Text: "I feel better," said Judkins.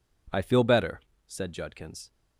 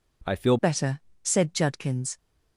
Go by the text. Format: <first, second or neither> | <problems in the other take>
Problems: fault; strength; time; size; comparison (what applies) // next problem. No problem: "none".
first | changes voice at "better"; from 0.5 s on; 1.6 s long